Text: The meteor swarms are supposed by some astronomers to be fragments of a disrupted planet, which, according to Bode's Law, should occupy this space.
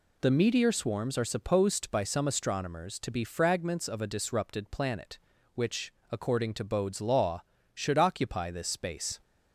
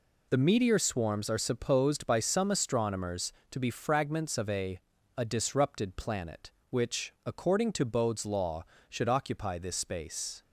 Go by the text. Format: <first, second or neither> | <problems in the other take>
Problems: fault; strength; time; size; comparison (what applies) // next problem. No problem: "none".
first | says "a" twice; at 5.1 s